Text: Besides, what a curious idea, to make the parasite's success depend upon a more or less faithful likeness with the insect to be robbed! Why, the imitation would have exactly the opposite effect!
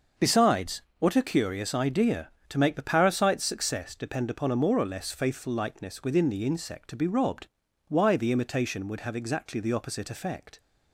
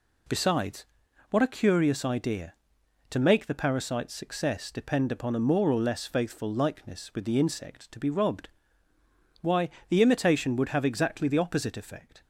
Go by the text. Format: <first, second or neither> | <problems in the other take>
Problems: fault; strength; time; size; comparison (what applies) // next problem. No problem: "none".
second | starts louder than the rest; noticeable; until 1.3 s; 6 dB // says "within" for "with"; at 6.0 s